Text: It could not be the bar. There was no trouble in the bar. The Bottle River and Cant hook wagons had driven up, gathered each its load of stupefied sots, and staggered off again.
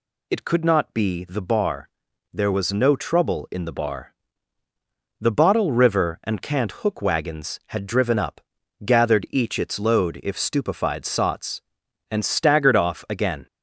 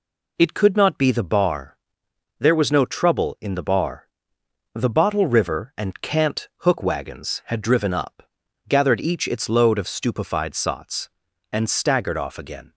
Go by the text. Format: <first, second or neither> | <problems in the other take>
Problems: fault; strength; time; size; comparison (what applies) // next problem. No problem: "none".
second | says "if" for "of"; at 10.2 s